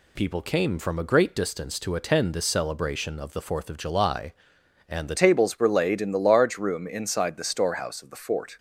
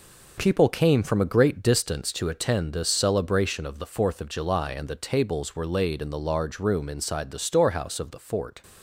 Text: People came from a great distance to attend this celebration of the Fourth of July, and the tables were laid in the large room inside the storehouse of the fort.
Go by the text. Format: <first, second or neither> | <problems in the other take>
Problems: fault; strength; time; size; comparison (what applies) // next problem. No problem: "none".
second | changes voice at "tables"; from 5.1 s on; 3.4 s long